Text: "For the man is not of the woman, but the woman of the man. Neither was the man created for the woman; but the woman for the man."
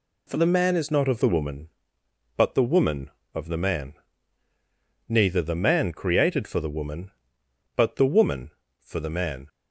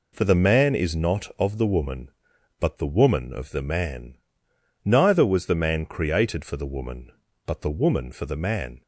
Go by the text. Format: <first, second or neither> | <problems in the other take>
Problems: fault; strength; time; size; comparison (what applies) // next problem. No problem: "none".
second | skips "was"; at 5.3 s